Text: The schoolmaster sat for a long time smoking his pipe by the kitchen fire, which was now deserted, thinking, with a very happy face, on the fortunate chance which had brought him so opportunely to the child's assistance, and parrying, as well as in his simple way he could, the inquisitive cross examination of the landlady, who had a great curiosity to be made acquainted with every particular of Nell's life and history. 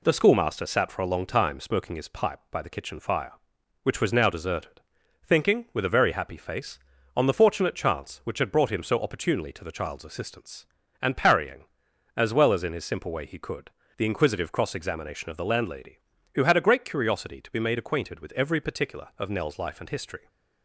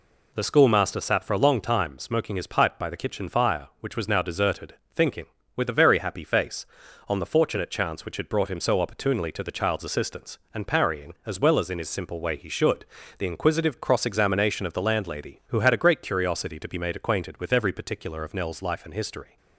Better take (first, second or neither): first